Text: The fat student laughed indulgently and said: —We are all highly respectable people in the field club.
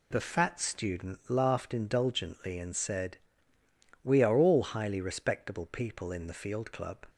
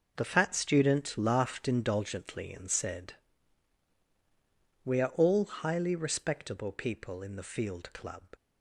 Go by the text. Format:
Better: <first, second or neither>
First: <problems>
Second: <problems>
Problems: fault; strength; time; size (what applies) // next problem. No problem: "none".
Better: neither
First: none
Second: none